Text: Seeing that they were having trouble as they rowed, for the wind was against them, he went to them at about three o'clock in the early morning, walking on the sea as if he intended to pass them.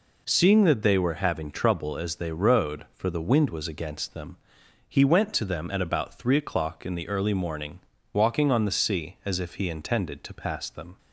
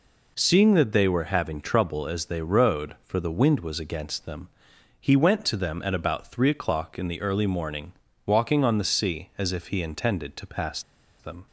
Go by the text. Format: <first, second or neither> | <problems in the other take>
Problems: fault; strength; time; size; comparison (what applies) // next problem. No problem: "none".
first | pauses between "pass" and "them"; at 10.8 s; 0.36 s long